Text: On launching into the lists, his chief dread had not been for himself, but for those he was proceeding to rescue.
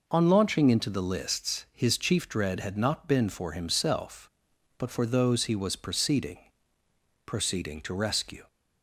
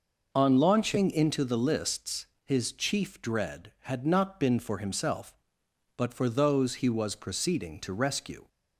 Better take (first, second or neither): second